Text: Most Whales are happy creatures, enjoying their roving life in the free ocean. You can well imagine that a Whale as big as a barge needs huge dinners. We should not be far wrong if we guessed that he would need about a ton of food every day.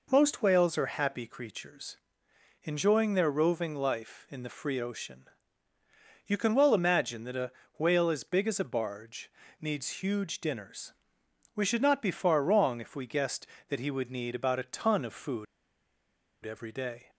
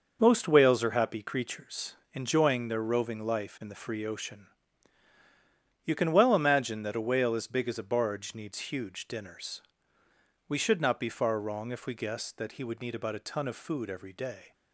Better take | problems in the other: second | pauses between "a" and "Whale"; slight; at 7.5 s; 0.26 s long // pauses between "barge" and "needs"; slight; at 9.3 s; 0.30 s long // pauses between "food" and "every"; at 15.4 s; 0.98 s long

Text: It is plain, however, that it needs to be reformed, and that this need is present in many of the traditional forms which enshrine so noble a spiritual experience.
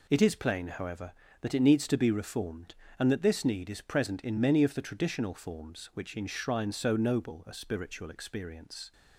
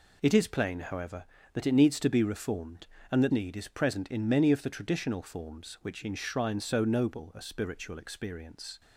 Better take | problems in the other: first | skips "this"; at 3.3 s

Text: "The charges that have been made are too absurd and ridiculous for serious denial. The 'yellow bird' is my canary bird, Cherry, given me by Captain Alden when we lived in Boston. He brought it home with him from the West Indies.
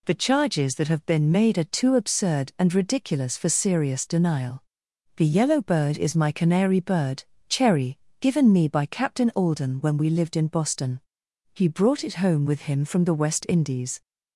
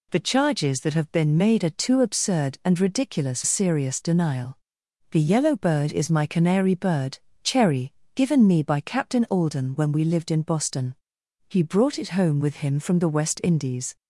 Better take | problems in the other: first | skips "for"; at 3.4 s

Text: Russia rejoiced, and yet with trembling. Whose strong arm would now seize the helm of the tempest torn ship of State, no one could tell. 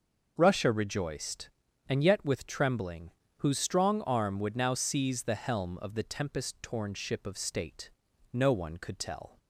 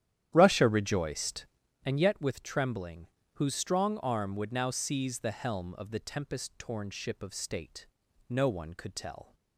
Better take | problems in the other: first | starts louder than the rest; strong; until 1.8 s; 11 dB

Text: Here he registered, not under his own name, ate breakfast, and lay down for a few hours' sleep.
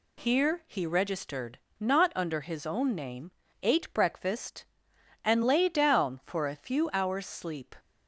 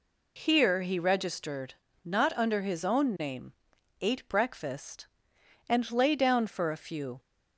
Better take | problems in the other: first | stops before "hours sleep"; at 7.1 s

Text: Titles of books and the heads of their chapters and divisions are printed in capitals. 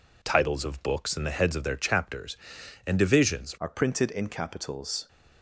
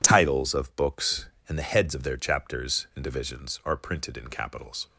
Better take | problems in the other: second | changes voice at "are"; from 3.5 s on; 1.5 s long

